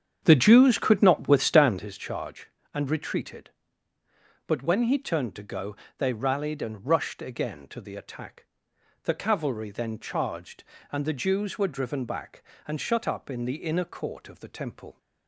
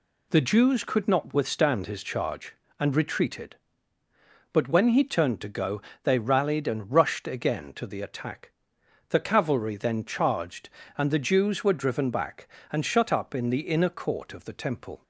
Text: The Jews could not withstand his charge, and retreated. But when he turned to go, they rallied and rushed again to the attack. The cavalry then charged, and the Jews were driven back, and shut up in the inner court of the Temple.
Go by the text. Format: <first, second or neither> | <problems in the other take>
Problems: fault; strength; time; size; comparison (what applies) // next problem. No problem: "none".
second | starts louder than the rest; strong; until 1.9 s; 8 dB